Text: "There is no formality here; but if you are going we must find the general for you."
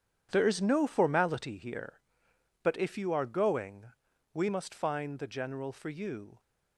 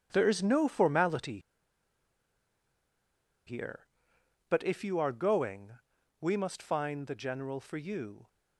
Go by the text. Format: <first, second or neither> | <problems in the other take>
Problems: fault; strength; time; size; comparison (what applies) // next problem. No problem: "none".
first | starts louder than the rest; strong; until 1.1 s; 9 dB; strong in the first // pauses between "formality" and "here"; strong; at 1.3 s; 2.0 s long // pauses between "going" and "we"; noticeable; at 5.7 s; 0.46 s long; also in the first